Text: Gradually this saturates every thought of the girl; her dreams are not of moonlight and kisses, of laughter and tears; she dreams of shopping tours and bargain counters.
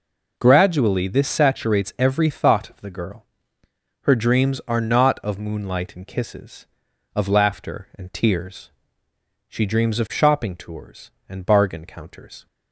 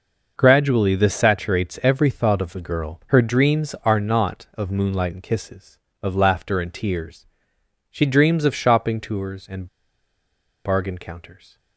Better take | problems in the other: first | pauses between "and" and "bargain"; at 9.6 s; 0.99 s long

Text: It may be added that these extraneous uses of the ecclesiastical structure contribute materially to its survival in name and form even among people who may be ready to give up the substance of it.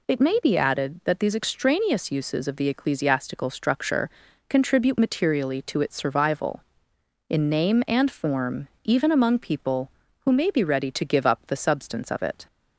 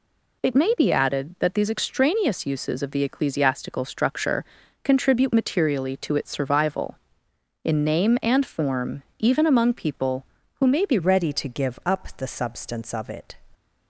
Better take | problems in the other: first | pauses between "structure" and "contribute"; at 4.4 s; 0.38 s long; also in the first // pauses between "form" and "even"; slight; at 9.0 s; 0.16 s long; slight in the first // changes voice at "ready"; from 10.9 s on; 2.4 s long

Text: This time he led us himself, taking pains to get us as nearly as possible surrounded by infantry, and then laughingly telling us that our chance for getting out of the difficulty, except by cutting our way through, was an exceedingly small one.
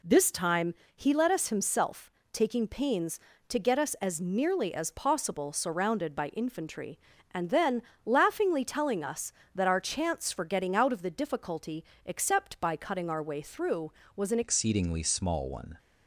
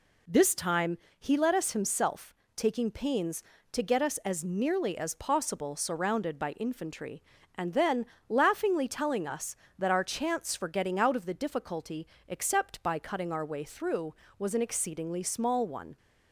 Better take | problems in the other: second | pauses between "time" and "he"; slight; at 0.7 s; 0.22 s long; slight in the second // pauses between "then" and "laughingly"; slight; at 7.8 s; 0.24 s long; slight in the second // changes voice at "exceedingly"; from 14.4 s on; 1.3 s long

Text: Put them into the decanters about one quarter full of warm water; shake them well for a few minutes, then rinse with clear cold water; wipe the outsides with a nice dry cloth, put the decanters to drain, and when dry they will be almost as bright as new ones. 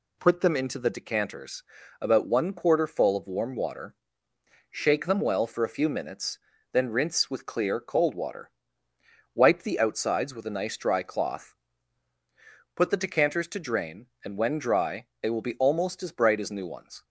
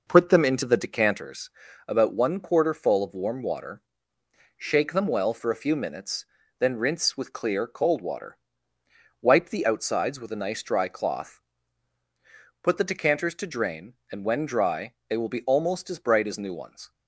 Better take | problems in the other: first | starts louder than the rest; noticeable; until 1.2 s; 5.5 dB // pauses between "decanters" and "about"; at 1.5 s; 0.38 s long; also in the first // pauses between "dry" and "they"; slight; at 14.9 s; 0.16 s long; slight in the first

